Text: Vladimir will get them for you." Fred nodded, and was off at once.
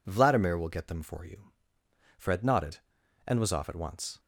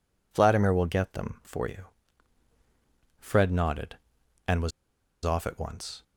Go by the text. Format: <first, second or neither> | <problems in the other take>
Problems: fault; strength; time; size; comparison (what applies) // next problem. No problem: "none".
first | pauses between "was" and "off"; noticeable; at 4.7 s; 0.54 s long